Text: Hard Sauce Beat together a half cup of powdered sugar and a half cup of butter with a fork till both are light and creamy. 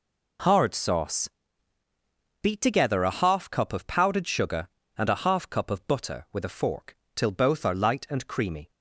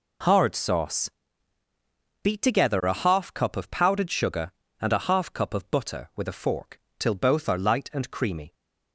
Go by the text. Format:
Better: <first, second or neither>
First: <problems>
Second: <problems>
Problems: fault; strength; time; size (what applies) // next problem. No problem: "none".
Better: neither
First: pauses between "Sauce" and "Beat"; at 1.2 s; 1.1 s long // pauses between "fork" and "till"; slight; at 6.9 s; 0.18 s long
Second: pauses between "Sauce" and "Beat"; at 1.0 s; 1.1 s long // pauses between "fork" and "till"; slight; at 6.7 s; 0.18 s long